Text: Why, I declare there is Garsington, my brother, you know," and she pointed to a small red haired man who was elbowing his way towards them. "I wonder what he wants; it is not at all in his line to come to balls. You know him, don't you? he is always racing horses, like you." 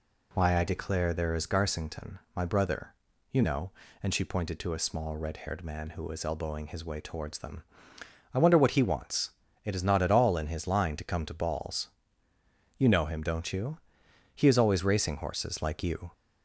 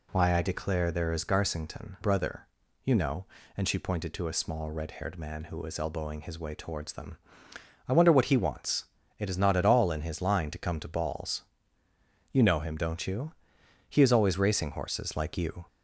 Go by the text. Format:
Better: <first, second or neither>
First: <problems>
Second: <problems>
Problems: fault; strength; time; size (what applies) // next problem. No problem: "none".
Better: first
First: none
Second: skips "my"; at 1.9 s